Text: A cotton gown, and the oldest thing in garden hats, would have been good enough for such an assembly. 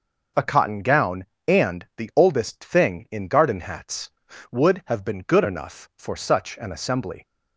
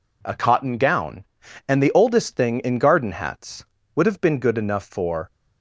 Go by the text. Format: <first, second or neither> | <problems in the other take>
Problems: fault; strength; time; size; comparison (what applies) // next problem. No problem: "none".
first | stops before "such an assembly"; at 5.2 s